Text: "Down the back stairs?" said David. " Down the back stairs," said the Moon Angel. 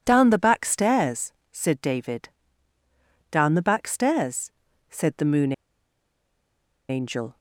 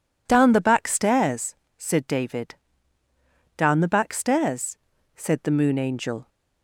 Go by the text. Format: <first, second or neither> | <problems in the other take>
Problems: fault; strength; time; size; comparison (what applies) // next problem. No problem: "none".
second | pauses between "Moon" and "Angel"; strong; at 5.5 s; 1.3 s long